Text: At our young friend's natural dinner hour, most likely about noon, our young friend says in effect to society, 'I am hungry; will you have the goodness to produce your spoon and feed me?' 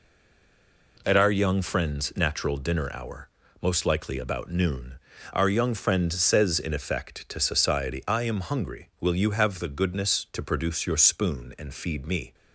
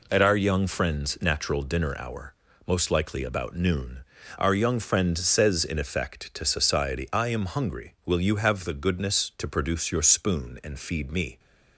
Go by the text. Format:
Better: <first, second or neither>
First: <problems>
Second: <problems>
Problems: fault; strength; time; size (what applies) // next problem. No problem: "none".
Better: second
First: stays silent before the first word; slight; until 0.9 s; 0.9 s long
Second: none